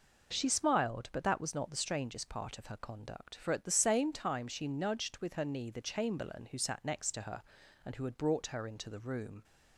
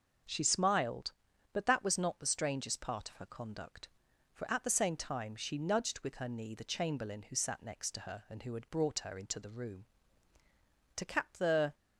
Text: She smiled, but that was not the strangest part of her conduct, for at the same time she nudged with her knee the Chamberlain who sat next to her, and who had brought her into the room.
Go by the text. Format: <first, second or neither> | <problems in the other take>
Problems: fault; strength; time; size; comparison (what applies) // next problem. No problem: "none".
first | goes on to say "To cap the"; noticeable; from 10.9 s on; 0.78 s long